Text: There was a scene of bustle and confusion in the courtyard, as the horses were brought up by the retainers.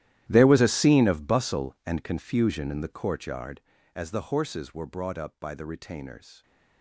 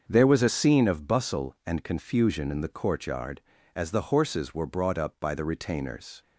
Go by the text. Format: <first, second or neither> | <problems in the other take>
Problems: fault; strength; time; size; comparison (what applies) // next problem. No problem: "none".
second | gets quieter; strong; throughout; 19.5 dB // starts louder than the rest; strong; until 1.3 s; 13 dB; also in the second